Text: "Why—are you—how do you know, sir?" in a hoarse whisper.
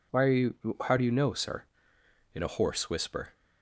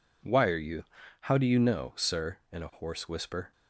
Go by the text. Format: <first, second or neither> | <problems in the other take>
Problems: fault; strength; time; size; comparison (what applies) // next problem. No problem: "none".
neither | none